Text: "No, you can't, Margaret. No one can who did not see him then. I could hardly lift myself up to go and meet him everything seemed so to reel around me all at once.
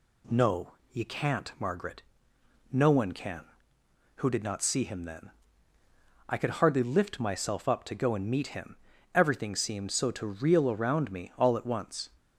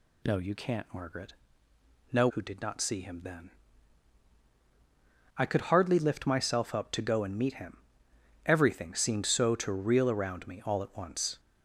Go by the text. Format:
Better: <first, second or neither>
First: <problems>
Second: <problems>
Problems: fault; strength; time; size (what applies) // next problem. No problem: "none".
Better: first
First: pauses between "him" and "everything"; slight; at 8.7 s; 0.36 s long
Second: skips "one can"; at 2.2 s // pauses between "him" and "everything"; noticeable; at 7.7 s; 0.70 s long